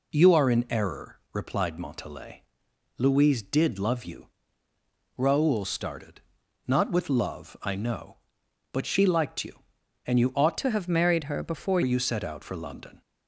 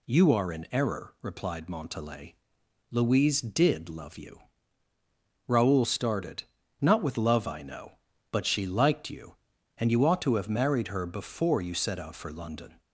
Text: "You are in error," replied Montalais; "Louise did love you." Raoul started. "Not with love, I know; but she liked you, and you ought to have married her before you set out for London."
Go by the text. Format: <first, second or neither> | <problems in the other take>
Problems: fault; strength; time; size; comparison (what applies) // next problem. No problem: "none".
second | changes voice from "to" to "before"; from 10.5 to 11.8 s; 1.3 s long